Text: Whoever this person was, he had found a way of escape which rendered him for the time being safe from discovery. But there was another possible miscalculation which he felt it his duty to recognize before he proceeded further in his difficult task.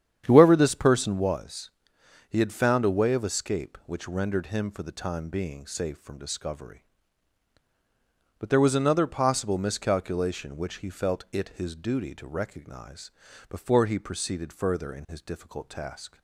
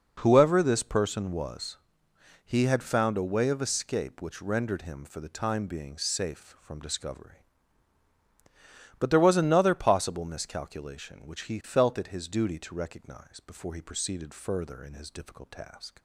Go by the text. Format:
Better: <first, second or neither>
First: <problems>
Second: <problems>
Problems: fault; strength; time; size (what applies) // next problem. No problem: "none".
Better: second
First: starts louder than the rest; strong; until 1.3 s; 9 dB // pauses between "recognize" and "before"; at 13.1 s; 0.40 s long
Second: none